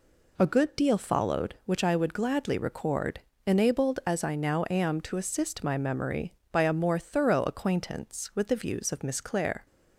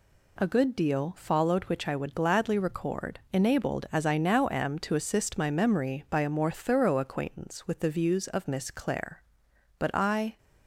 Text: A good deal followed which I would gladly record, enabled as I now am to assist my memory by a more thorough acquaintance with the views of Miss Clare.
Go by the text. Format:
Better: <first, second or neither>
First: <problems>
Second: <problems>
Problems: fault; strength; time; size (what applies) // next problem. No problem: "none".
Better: first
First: none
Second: goes on to say "But I"; from 9.7 s on; 0.58 s long